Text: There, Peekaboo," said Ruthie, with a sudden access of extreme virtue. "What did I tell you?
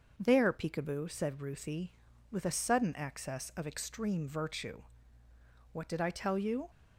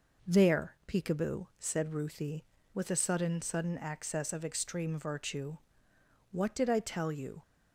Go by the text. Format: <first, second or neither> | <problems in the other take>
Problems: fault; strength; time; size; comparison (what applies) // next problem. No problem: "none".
first | says "sudden" twice; at 3.4 s